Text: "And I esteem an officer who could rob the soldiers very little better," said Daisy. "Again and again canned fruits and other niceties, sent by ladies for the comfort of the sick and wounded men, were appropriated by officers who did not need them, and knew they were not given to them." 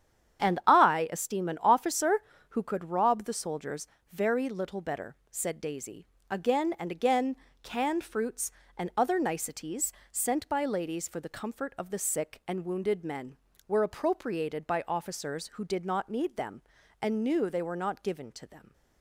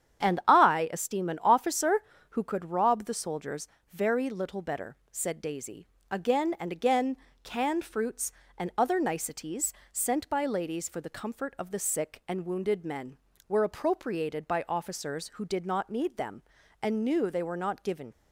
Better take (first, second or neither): first